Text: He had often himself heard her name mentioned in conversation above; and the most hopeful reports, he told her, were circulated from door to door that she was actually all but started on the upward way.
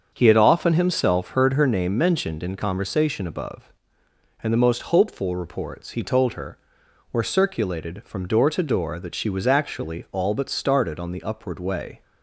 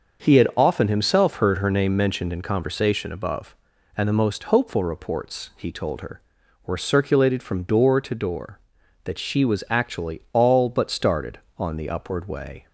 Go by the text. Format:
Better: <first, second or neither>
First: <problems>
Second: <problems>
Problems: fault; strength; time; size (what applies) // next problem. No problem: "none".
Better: neither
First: starts louder than the rest; until 1.1 s; 7 dB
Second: starts louder than the rest; until 1.2 s; 6 dB